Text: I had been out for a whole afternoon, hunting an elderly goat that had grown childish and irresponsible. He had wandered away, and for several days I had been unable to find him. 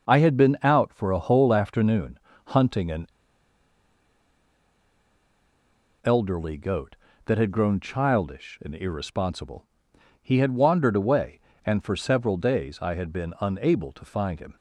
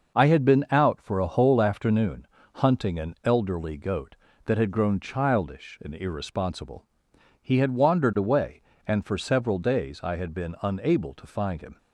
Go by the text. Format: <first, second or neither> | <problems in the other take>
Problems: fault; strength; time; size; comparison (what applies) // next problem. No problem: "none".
second | pauses between "an" and "elderly"; strong; at 3.0 s; 2.9 s long